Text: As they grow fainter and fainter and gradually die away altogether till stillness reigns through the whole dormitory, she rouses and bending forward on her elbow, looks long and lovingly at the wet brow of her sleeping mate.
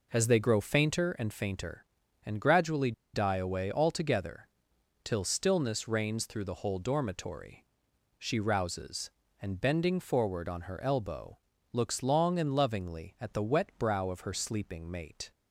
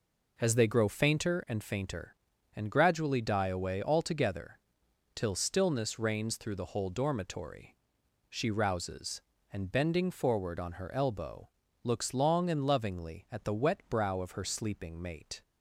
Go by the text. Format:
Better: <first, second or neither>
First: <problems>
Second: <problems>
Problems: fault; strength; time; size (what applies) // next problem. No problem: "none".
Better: second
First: pauses between "gradually" and "die"; slight; at 2.9 s; 0.22 s long // pauses between "altogether" and "till"; noticeable; at 4.4 s; 0.56 s long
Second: pauses between "altogether" and "till"; noticeable; at 4.5 s; 0.56 s long